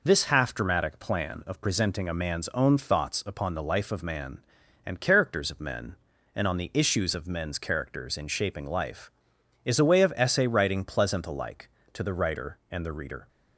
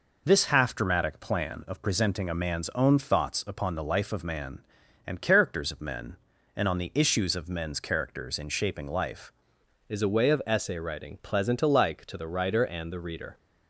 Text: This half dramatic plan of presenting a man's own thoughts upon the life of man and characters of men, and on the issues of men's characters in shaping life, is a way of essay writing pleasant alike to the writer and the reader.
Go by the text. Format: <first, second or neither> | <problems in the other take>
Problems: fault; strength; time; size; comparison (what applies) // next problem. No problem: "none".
first | changes voice at "is"; from 9.8 s on; 3.5 s long